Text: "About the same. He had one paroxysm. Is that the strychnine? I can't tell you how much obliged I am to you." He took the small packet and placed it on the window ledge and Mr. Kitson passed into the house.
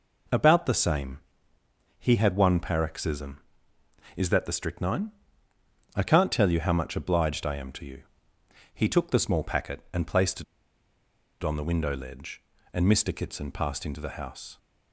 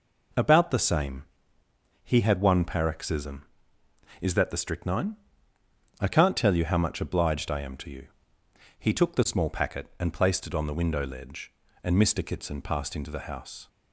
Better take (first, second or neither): second